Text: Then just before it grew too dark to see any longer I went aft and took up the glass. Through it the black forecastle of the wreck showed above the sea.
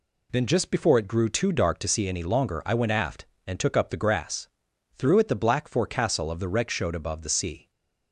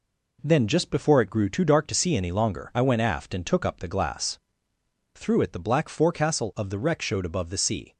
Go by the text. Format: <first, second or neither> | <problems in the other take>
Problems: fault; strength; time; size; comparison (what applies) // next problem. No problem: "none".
second | says "grass" for "glass"; at 3.9 s // stays silent after the last word; slight; from 7.6 s on; 0.5 s long